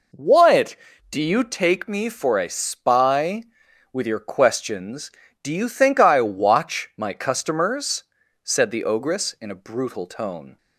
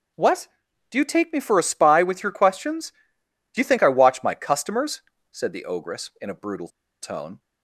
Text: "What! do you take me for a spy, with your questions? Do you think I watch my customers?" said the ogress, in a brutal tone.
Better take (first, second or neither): first